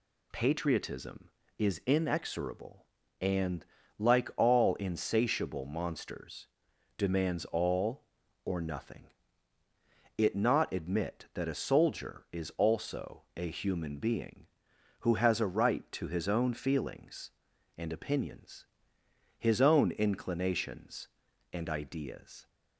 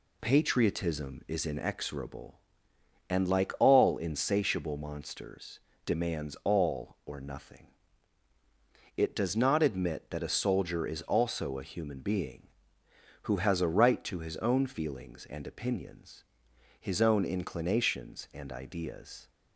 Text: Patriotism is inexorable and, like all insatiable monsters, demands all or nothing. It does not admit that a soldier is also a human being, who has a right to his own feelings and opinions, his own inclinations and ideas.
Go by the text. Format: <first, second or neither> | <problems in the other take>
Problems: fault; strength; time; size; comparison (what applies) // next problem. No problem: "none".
second | skips "does"; at 10.3 s